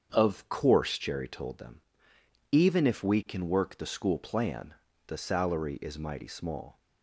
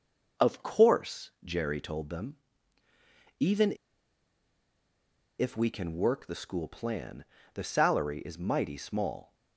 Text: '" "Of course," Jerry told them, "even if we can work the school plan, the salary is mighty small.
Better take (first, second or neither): first